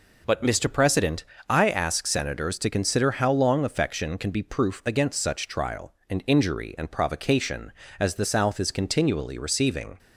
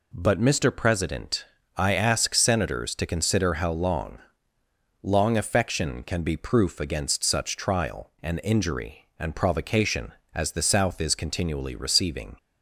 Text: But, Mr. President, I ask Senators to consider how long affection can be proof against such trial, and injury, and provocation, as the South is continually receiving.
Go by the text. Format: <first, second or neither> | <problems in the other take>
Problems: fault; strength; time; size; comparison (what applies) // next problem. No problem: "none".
first | says "long" twice; at 5.0 s